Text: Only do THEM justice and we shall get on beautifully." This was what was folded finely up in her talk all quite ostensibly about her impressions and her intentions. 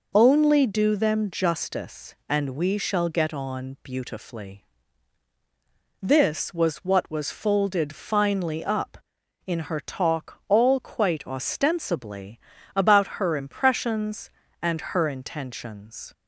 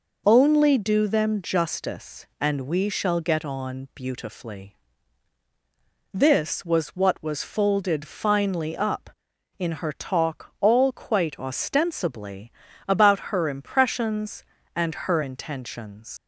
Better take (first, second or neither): first